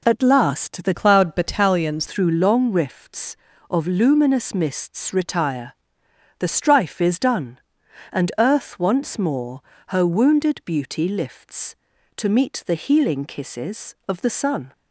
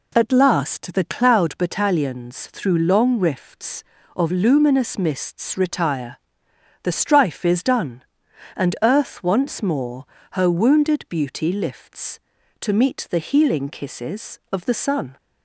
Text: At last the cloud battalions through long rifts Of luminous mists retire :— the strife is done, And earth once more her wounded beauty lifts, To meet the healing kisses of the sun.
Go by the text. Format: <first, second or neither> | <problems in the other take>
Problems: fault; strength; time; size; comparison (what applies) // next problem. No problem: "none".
second | changes voice from "cloud" to "battalions"; from 0.9 to 2.0 s; 1.1 s long // pauses between "more" and "her"; slight; at 9.6 s; 0.26 s long; slight in the second